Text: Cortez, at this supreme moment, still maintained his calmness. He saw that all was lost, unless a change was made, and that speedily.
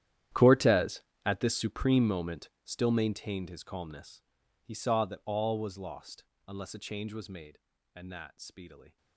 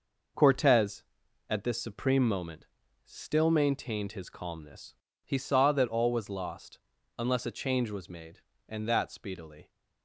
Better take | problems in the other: second | gets quieter; strong; throughout; 18.5 dB

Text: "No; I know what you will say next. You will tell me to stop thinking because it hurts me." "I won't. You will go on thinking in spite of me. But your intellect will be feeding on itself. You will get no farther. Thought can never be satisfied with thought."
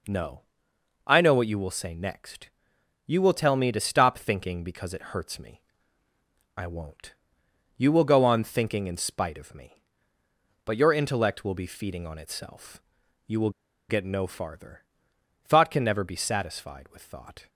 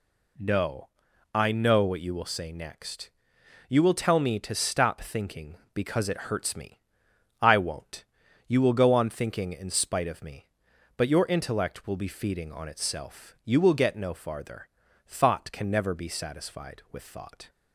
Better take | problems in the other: second | pauses between "will" and "get"; at 13.4 s; 0.39 s long

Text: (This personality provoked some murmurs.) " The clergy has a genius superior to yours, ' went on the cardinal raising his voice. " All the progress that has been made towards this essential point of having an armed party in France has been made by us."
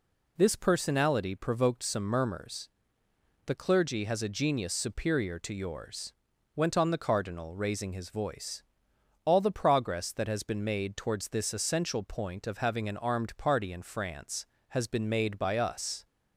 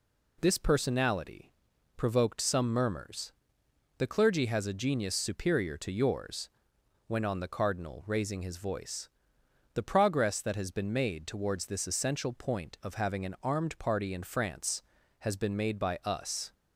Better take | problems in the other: first | pauses between "personality" and "provoked"; noticeable; at 1.5 s; 0.46 s long // skips "All"; at 9.7 s

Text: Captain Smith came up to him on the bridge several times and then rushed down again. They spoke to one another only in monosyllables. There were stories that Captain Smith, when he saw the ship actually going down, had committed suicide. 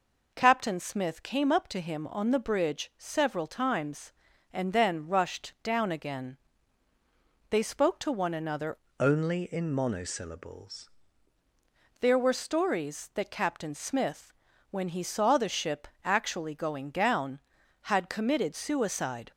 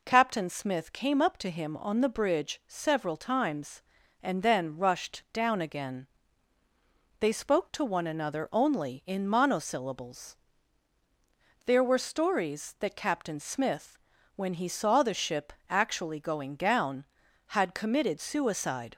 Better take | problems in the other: second | changes voice from "only" to "monosyllables"; from 9.0 to 10.8 s; 1.8 s long // pauses between "ship" and "actually"; slight; at 15.8 s; 0.16 s long; slight in the second

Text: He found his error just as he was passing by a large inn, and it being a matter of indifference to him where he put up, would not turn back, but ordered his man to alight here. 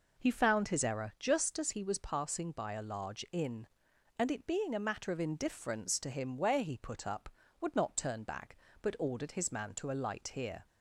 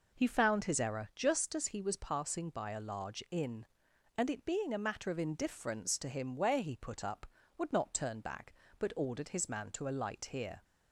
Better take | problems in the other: neither | none

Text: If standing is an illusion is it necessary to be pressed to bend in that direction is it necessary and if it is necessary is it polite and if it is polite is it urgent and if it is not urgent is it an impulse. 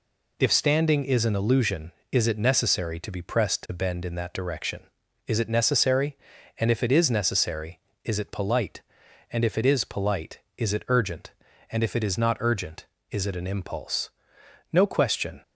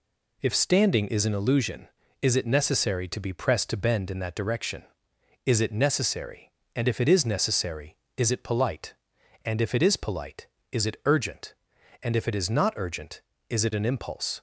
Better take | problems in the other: second | goes on to say "No question"; noticeable; from 14.7 s on; 0.68 s long

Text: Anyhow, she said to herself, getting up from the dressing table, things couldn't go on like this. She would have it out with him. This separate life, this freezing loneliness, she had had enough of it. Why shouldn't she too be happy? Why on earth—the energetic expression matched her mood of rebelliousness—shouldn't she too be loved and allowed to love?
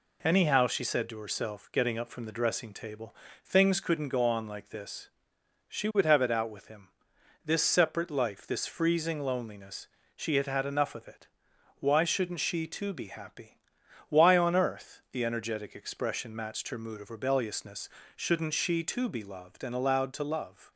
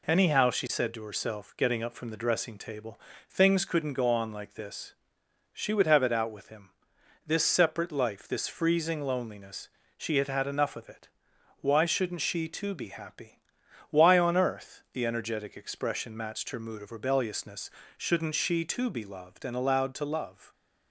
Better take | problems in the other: neither | none

